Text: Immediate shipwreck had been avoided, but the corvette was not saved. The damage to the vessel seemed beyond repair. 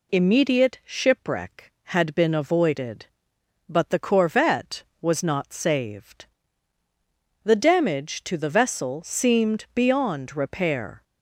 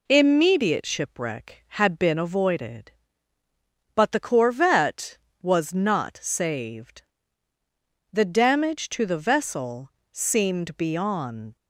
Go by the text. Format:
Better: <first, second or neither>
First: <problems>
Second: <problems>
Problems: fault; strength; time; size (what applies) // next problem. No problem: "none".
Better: first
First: none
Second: pauses between "vessel" and "seemed"; slight; at 9.8 s; 0.22 s long // stops before "repair"; at 11.5 s